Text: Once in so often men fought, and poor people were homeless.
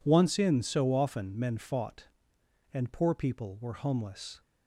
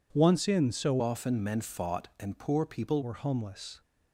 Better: first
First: none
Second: changes voice from "often" to "people"; from 0.9 to 3.0 s; 2.1 s long

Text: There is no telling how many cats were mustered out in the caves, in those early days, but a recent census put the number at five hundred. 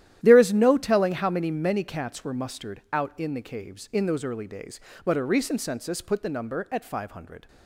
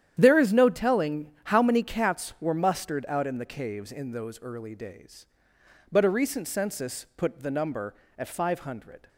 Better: second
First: starts louder than the rest; strong; until 1.2 s; 12 dB // says "many" twice; at 1.4 s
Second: starts louder than the rest; strong; until 1.2 s; 10 dB

